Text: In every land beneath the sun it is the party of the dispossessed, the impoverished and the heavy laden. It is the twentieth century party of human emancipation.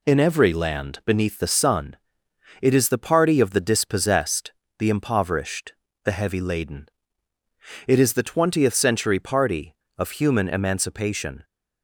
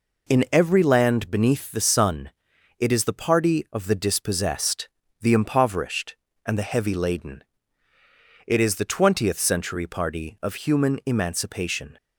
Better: second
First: pauses between "sun" and "it"; noticeable; at 1.9 s; 0.64 s long // skips "and"; at 5.8 s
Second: pauses between "sun" and "it"; noticeable; at 2.3 s; 0.48 s long

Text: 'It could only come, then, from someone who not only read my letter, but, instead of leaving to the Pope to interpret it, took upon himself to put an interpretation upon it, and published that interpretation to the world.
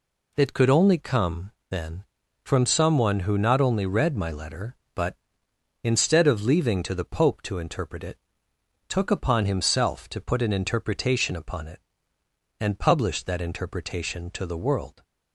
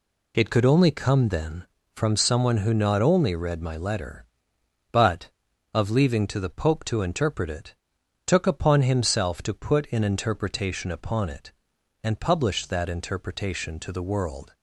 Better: first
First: none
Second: skips "instead"; at 5.5 s

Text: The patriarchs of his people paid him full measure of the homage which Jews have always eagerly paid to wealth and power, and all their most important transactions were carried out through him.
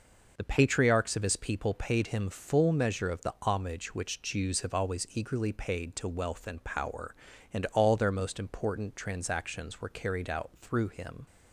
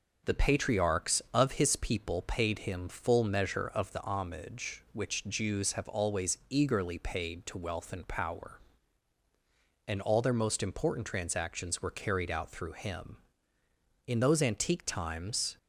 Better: first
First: none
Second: goes on to say "In those antique times"; from 14.0 s on; 1.5 s long

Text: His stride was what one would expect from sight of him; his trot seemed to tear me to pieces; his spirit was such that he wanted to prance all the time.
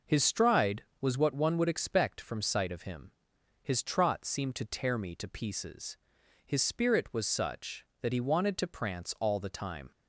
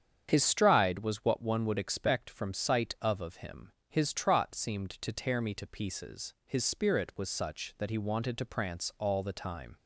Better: first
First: none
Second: starts louder than the rest; strong; until 1.3 s; 8 dB // says "of" twice; at 3.1 s

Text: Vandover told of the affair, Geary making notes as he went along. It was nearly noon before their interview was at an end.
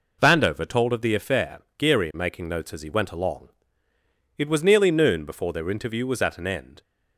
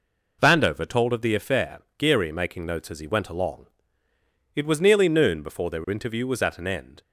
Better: neither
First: none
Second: none

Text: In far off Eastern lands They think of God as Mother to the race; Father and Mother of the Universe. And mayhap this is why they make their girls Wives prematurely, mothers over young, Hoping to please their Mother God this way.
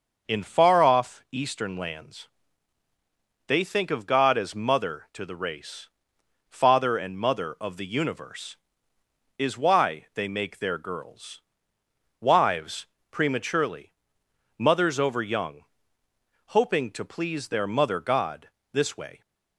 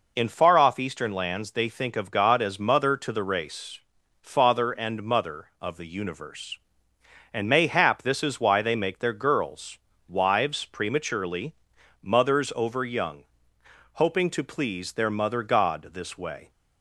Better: second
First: starts louder than the rest; noticeable; until 1.3 s; 6 dB // pauses between "lands" and "They"; at 2.2 s; 1.1 s long // skips "And mayhap this"; at 8.9 s // pauses between "girls" and "Wives"; noticeable; at 11.4 s; 0.78 s long // pauses between "Wives" and "prematurely"; slight; at 12.8 s; 0.24 s long // pauses between "God" and "this"; slight; at 18.4 s; 0.24 s long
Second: pauses between "girls" and "Wives"; slight; at 9.7 s; 0.30 s long

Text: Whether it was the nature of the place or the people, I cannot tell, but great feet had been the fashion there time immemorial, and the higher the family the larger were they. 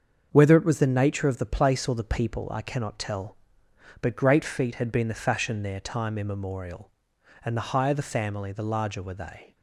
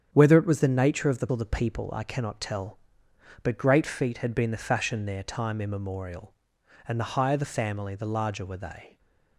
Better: first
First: starts louder than the rest; until 1.3 s; 7 dB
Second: starts louder than the rest; strong; until 1.1 s; 8.5 dB // skips "place"; at 1.2 s

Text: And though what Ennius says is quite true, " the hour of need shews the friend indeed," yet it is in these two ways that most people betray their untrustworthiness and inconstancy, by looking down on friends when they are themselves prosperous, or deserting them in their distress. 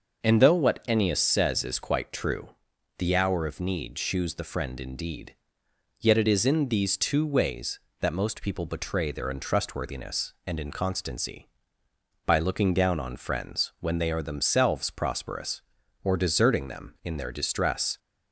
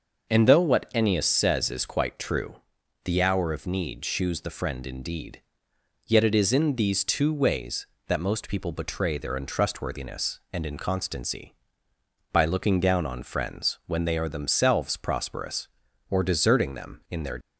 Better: first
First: starts louder than the rest; until 1.2 s; 6.5 dB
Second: starts louder than the rest; until 1.3 s; 6.5 dB // stops before "distress"; at 17.4 s

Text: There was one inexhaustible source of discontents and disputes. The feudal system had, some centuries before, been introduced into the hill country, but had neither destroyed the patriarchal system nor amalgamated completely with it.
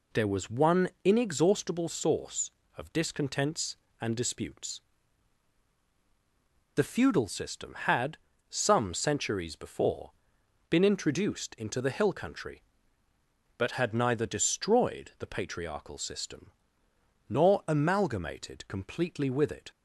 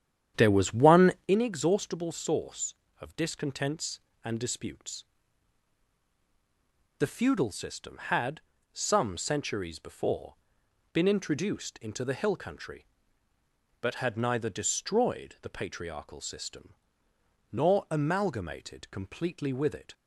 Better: first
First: pauses between "one" and "inexhaustible"; slight; at 0.8 s; 0.16 s long // pauses between "system" and "nor"; noticeable; at 16.5 s; 0.78 s long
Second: starts louder than the rest; strong; until 1.3 s; 9.5 dB // pauses between "one" and "inexhaustible"; slight; at 1.1 s; 0.16 s long // pauses between "system" and "nor"; noticeable; at 16.7 s; 0.78 s long

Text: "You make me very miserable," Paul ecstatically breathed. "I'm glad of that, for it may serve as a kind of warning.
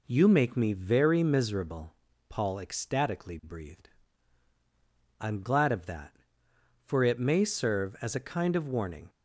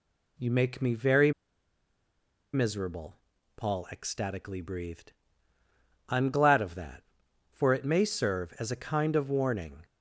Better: first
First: none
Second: pauses between "very" and "miserable"; at 1.3 s; 1.2 s long

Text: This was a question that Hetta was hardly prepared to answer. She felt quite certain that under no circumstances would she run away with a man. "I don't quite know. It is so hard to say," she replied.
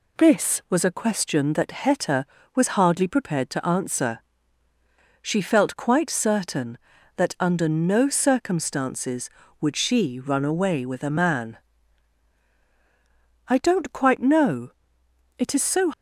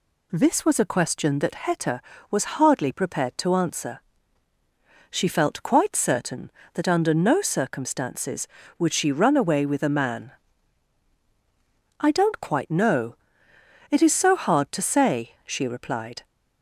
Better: second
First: stops before "hard to say she replied"; at 15.9 s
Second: none

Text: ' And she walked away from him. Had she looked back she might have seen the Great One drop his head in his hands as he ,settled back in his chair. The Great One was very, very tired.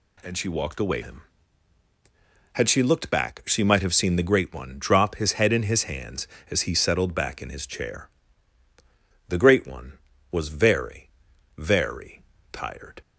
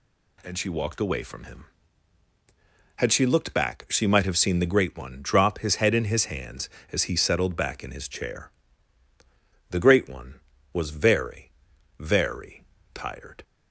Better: second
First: skips "from"; at 1.0 s // pauses between "very" and "tired"; slight; at 12.2 s; 0.28 s long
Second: pauses between "very" and "tired"; slight; at 12.6 s; 0.28 s long

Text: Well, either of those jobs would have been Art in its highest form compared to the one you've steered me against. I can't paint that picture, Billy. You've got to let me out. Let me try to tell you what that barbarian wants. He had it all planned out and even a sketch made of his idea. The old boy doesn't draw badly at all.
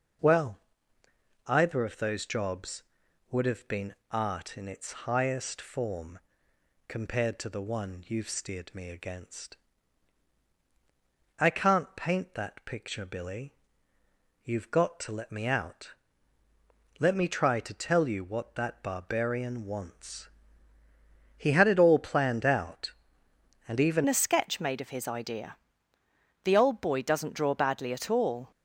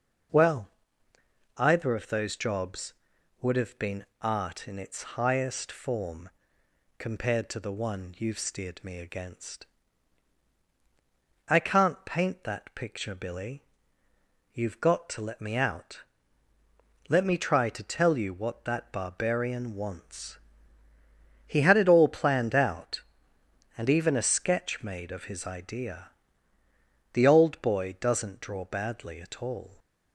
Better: second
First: pauses between "been" and "Art"; slight; at 3.9 s; 0.16 s long // pauses between "form" and "compared"; noticeable; at 6.1 s; 0.70 s long // changes voice at "a"; from 24.0 s on; 4.5 s long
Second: pauses between "been" and "Art"; slight; at 4.0 s; 0.16 s long // pauses between "form" and "compared"; noticeable; at 6.2 s; 0.70 s long

